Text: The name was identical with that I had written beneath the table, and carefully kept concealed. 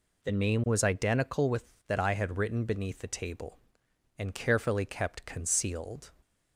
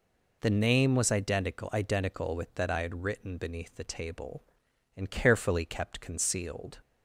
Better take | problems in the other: first | says "identical" twice; at 1.7 s

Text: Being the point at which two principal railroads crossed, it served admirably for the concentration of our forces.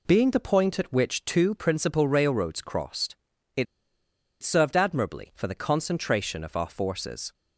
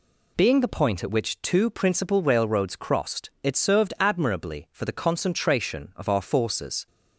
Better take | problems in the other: second | pauses between "it" and "served"; noticeable; at 3.6 s; 0.77 s long

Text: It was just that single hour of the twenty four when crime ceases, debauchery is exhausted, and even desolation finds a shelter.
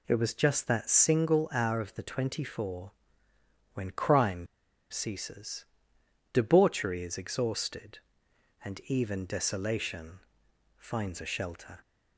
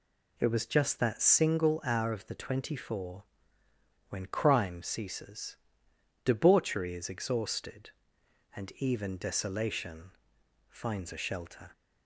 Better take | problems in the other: second | pauses between "four" and "when"; noticeable; at 2.9 s; 0.82 s long; noticeable in the second // pauses between "crime" and "ceases"; at 4.4 s; 0.43 s long // pauses between "desolation" and "finds"; noticeable; at 10.2 s; 0.58 s long; noticeable in the second

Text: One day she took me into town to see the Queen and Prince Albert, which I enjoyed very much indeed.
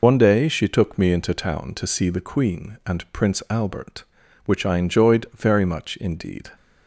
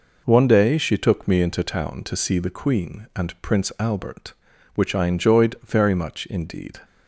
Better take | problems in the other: second | loses the start of "One"; at 0.0 s; 80 ms

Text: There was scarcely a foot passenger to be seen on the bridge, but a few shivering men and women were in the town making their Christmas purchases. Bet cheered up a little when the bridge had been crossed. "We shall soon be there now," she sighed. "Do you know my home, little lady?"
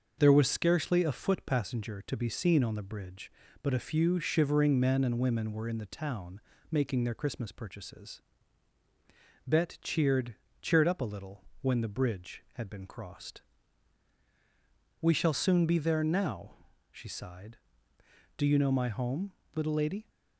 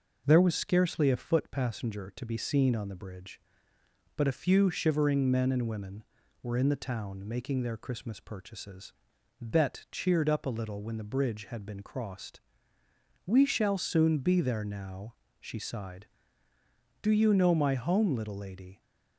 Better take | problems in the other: second | starts louder than the rest; noticeable; until 1.2 s; 6 dB // pauses between "town" and "making"; slight; at 6.4 s; 0.28 s long // says "cheered" twice; at 10.6 s // pauses between "little" and "when"; slight; at 11.4 s; 0.16 s long

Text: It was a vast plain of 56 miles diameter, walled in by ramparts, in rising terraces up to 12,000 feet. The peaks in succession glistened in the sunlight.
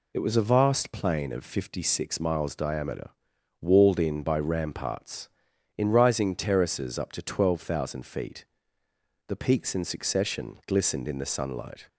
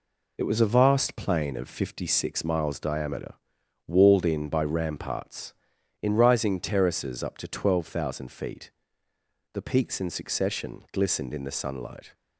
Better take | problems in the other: first | gets quieter; throughout; 6 dB

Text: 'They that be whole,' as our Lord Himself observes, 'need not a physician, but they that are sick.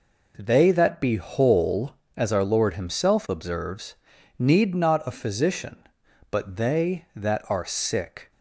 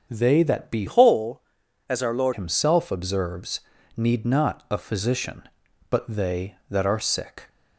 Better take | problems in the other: first | starts louder than the rest; strong; until 1.1 s; 7.5 dB // changes voice from "whole" to "Lord"; from 0.8 to 2.3 s; 1.5 s long

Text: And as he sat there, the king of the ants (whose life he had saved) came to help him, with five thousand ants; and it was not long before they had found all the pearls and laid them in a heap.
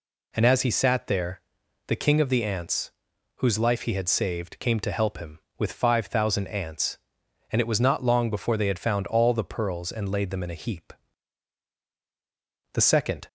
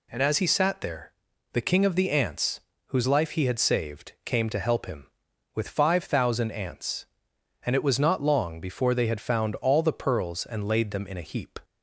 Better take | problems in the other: second | goes on to say "The second"; from 12.7 s on; 0.54 s long

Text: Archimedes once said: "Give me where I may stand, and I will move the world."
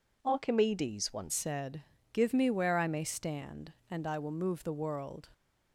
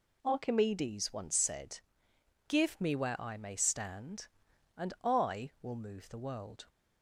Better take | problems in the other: second | changes voice at "said"; from 1.3 s on; 3.9 s long

